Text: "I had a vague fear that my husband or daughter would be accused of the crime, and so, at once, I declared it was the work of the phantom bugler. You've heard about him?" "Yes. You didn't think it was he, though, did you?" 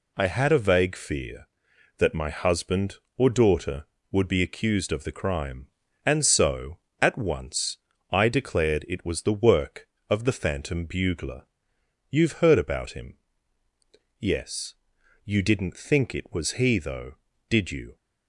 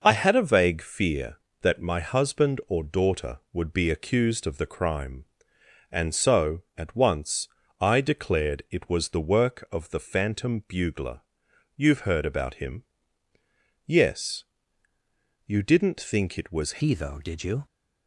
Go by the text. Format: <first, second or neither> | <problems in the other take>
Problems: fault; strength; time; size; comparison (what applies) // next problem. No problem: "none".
first | changes voice at "he"; from 16.8 s on; 0.8 s long